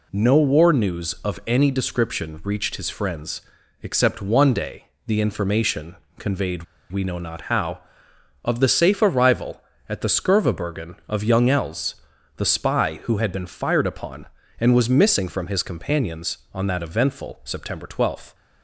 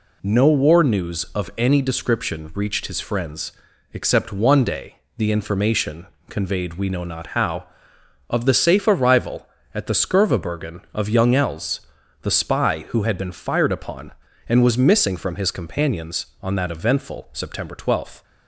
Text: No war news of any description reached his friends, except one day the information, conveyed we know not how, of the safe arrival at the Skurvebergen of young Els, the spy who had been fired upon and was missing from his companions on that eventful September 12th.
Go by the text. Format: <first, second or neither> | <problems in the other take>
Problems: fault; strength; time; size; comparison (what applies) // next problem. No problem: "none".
second | pauses between "day" and "the"; slight; at 4.8 s; 0.18 s long; slight in the second // pauses between "conveyed" and "we"; slight; at 6.6 s; 0.27 s long